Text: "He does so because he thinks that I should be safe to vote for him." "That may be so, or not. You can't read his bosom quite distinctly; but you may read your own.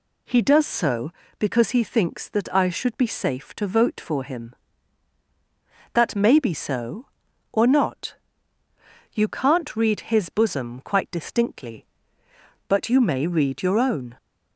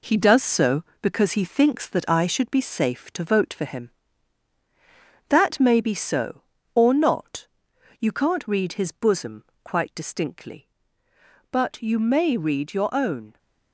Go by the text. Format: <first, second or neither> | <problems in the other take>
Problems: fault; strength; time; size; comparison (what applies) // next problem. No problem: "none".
first | gets quieter; throughout; 6 dB // pauses between "bosom" and "quite"; slight; at 9.4 s; 0.20 s long